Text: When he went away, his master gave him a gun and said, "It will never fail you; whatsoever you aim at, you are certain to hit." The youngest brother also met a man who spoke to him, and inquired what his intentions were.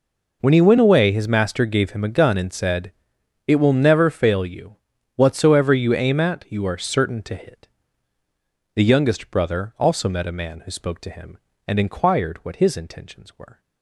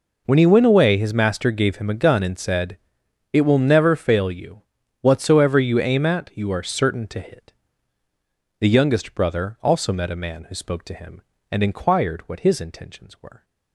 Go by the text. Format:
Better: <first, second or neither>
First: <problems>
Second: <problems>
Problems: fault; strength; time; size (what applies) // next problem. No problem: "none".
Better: neither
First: none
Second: none